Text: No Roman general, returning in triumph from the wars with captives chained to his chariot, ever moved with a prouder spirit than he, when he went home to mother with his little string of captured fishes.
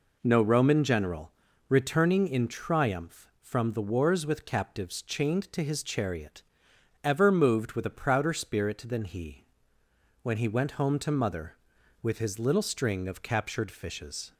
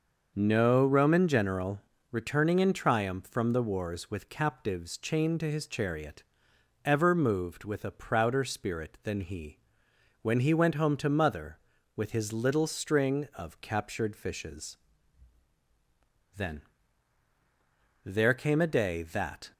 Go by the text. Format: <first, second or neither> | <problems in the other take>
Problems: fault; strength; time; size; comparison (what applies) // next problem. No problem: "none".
first | starts louder than the rest; noticeable; until 1.3 s; 6 dB // goes on to say "Then there came a day that"; strong; from 16.3 s on; 3.1 s long